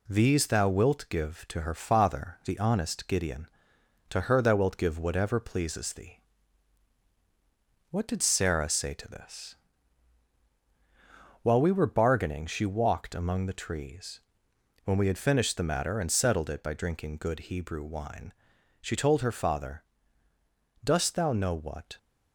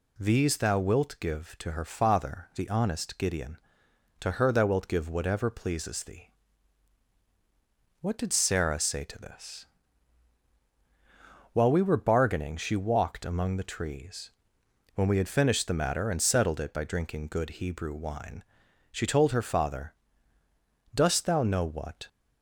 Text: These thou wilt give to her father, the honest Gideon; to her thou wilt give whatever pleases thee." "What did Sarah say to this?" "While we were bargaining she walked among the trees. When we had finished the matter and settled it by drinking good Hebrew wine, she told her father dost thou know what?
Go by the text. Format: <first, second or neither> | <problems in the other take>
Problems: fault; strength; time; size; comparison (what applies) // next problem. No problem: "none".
second | gets quieter; slight; throughout; 3 dB // pauses between "father" and "dost"; at 19.8 s; 1.0 s long; also in the second